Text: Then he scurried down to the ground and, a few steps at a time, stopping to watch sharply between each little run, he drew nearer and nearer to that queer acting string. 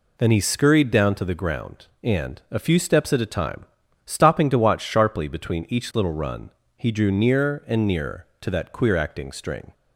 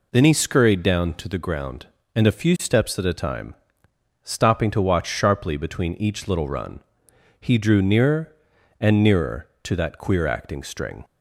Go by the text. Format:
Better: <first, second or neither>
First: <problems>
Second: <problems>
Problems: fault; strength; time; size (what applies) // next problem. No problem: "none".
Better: neither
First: none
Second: none